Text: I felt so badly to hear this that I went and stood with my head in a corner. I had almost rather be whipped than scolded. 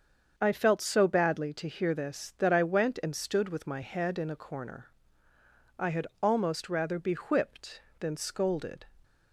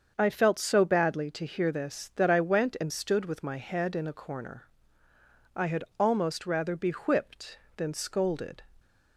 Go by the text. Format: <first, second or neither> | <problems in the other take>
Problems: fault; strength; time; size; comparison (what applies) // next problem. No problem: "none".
neither | starts louder than the rest; the same in both // pauses between "had" and "almost"; slight; the same in both